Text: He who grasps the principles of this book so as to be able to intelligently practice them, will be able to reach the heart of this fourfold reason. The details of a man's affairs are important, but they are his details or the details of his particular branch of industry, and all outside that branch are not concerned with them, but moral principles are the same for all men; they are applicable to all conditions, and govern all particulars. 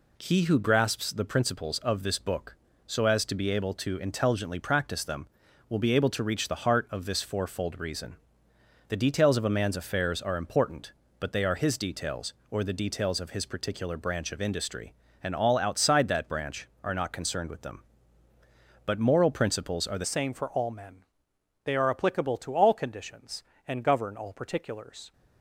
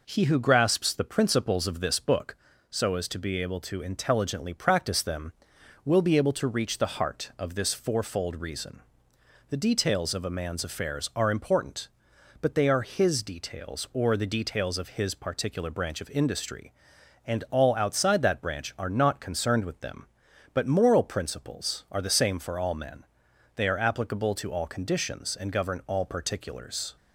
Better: second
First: changes voice at "same"; from 20.0 s on; 5.1 s long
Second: none

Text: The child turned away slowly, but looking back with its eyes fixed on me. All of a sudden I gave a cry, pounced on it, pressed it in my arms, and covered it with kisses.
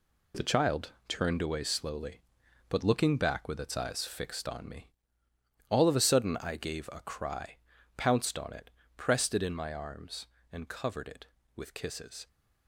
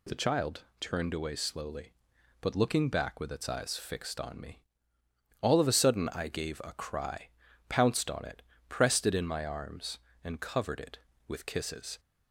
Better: second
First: gets quieter; strong; throughout; 8.5 dB // pauses between "child" and "turned"; slight; at 0.9 s; 0.16 s long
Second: pauses between "child" and "turned"; slight; at 0.6 s; 0.16 s long

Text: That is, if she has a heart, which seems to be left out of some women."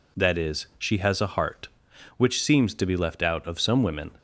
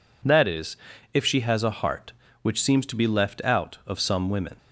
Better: second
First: skips "if"; at 0.7 s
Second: none

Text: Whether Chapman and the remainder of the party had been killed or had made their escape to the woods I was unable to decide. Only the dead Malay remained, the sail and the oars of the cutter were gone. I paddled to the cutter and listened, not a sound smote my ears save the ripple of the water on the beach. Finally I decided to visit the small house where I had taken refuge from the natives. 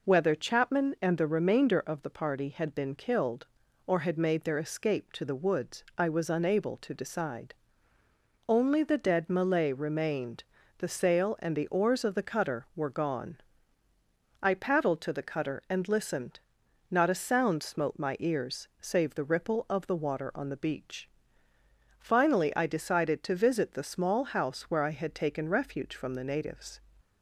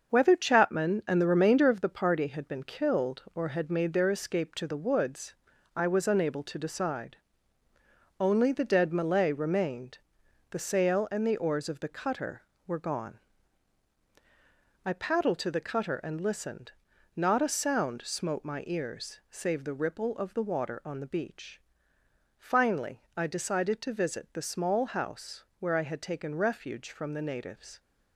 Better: first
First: none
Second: gets quieter; throughout; 6.5 dB // pauses between "woods" and "I"; at 5.3 s; 0.42 s long // pauses between "house" and "where"; slight; at 25.4 s; 0.16 s long

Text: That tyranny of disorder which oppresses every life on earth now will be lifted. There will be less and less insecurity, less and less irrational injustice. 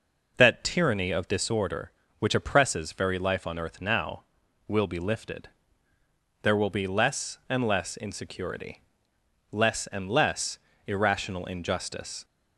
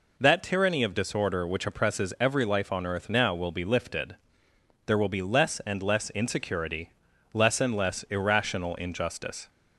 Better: second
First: says "very" for "every"; at 2.9 s // pauses between "less" and "irrational"; slight; at 10.5 s; 0.28 s long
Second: none

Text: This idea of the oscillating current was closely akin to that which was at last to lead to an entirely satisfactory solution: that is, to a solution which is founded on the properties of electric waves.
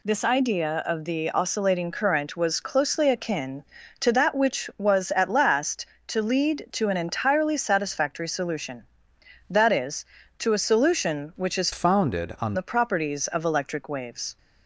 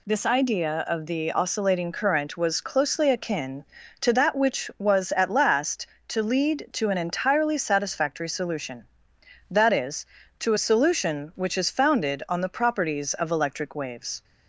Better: second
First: changes voice from "founded" to "on"; from 11.7 to 12.5 s; 0.8 s long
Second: none

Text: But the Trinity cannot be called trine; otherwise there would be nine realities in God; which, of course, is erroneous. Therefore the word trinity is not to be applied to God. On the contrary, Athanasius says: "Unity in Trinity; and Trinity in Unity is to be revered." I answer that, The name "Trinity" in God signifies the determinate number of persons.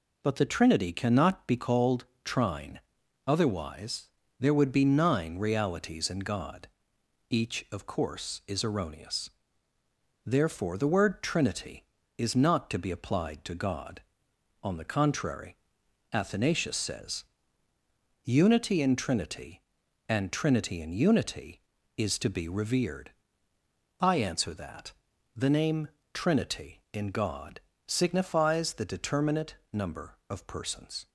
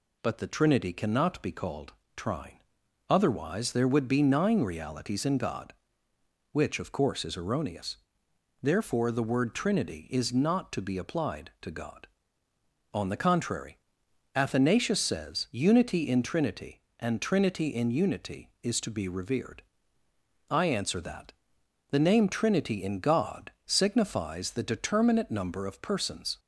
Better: second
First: pauses between "called" and "trine"; slight; at 2.0 s; 0.20 s long // pauses between "otherwise" and "there"; slight; at 4.0 s; 0.30 s long // says "each" for "which"; at 7.2 s // pauses between "name" and "Trinity"; slight; at 25.8 s; 0.24 s long // pauses between "God" and "signifies"; slight; at 27.6 s; 0.26 s long // pauses between "determinate" and "number"; slight; at 29.5 s; 0.18 s long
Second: pauses between "called" and "trine"; slight; at 1.9 s; 0.24 s long

